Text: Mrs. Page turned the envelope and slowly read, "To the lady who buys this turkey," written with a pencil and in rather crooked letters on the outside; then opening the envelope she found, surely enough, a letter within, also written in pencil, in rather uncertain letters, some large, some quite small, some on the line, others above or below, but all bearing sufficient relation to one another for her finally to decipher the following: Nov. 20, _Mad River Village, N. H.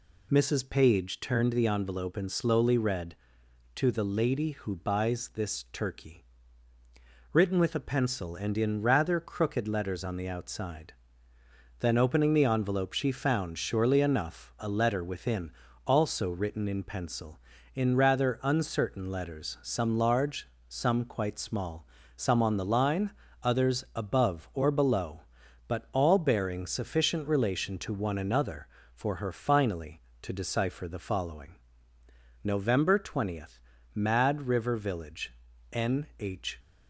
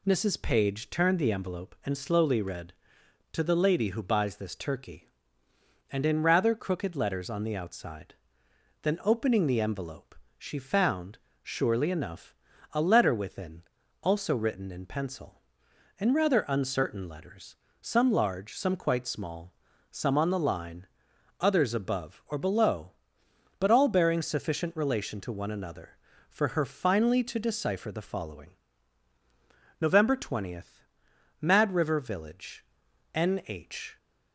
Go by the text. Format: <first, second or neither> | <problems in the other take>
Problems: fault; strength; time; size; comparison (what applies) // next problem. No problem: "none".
first | skips "written with a pencil"; at 5.4 s // pauses between "envelope" and "she"; slight; at 10.1 s; 0.24 s long